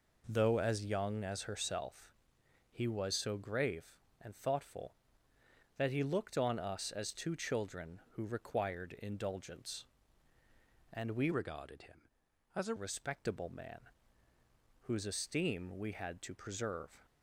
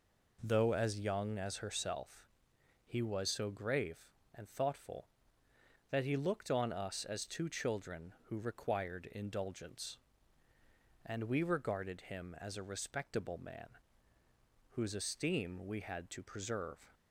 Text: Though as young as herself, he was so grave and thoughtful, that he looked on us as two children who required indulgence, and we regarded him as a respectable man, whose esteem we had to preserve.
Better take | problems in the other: second | changes voice from "regarded" to "a"; from 11.3 to 12.7 s; 1.4 s long

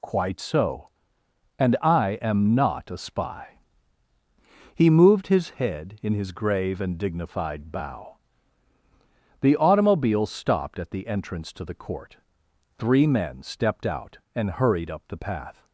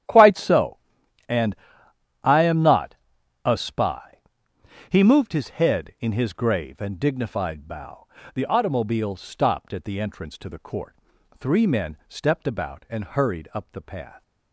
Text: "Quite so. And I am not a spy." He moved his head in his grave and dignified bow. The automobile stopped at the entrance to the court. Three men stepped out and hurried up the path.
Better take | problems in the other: first | starts louder than the rest; strong; until 2.2 s; 10.5 dB // pauses between "And" and "I"; noticeable; at 1.5 s; 0.66 s long // pauses between "not" and "a"; noticeable; at 2.9 s; 0.50 s long // says "about" for "out"; at 12.4 s

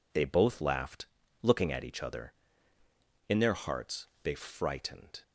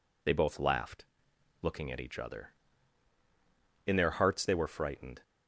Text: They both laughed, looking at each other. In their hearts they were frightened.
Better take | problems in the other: second | pauses between "hearts" and "they"; slight; at 4.0 s; 0.16 s long // skips "were"; at 4.3 s

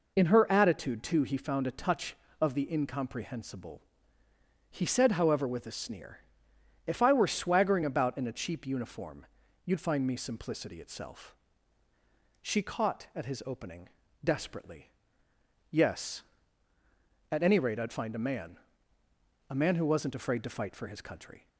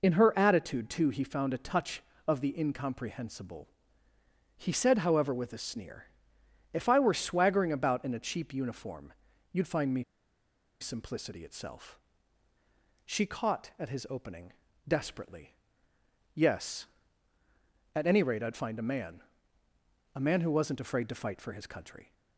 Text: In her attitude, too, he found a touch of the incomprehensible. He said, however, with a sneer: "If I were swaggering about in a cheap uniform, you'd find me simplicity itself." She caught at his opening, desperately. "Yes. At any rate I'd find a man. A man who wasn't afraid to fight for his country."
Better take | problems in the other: first | pauses between "me" and "simplicity"; noticeable; at 10.0 s; 0.78 s long

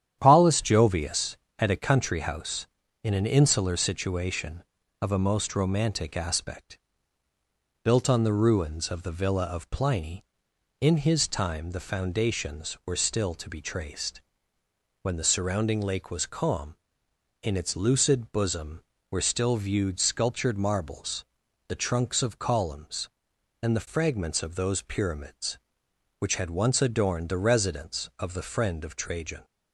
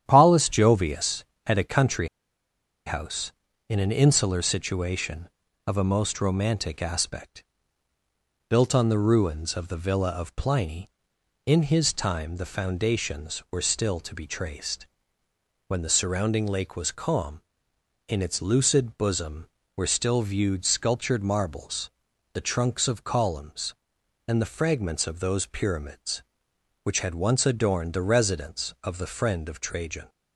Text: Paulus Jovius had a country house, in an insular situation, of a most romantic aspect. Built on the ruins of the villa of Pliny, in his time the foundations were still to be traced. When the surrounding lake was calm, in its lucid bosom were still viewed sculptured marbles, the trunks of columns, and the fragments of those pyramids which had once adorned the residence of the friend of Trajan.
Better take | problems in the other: first | starts louder than the rest; strong; until 1.0 s; 10 dB; strong in the first // pauses between "country" and "house"; noticeable; at 2.0 s; 0.79 s long

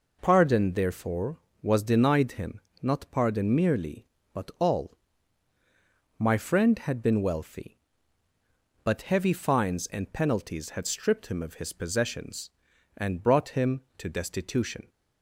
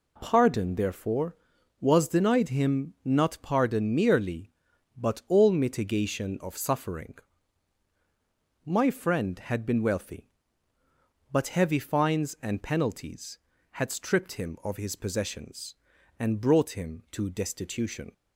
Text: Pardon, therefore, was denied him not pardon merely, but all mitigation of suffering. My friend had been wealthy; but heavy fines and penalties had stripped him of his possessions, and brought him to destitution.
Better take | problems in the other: second | pauses between "him" and "not"; slight; at 2.6 s; 0.22 s long // skips "mitigation of suffering"; at 5.5 s

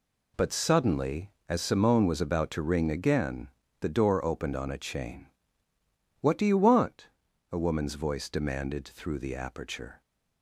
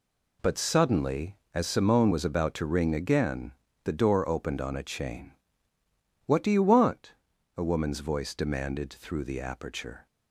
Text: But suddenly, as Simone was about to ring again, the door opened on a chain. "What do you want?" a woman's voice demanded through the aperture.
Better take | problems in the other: neither | none

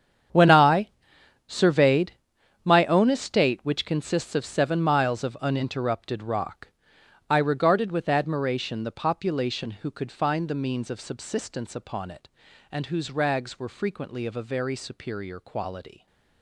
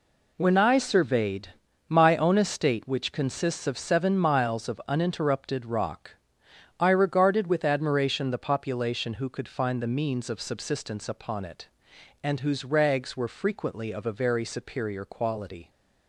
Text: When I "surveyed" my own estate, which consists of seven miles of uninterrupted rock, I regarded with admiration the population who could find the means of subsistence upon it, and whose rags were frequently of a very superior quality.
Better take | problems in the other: second | gets quieter; strong; throughout; 15.5 dB // pauses between "I" and "surveyed"; noticeable; at 0.8 s; 0.58 s long // pauses between "surveyed" and "my"; noticeable; at 2.1 s; 0.52 s long; also in the second

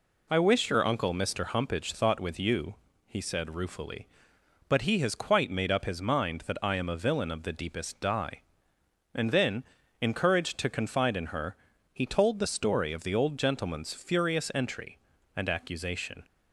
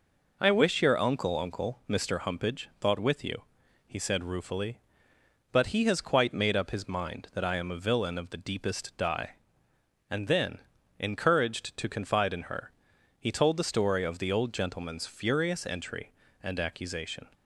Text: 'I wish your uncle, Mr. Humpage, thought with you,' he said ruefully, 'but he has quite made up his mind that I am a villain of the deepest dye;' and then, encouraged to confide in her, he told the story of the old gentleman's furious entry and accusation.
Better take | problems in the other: first | says "uncle" twice; at 1.3 s

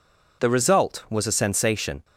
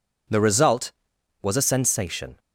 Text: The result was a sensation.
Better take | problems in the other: neither | none

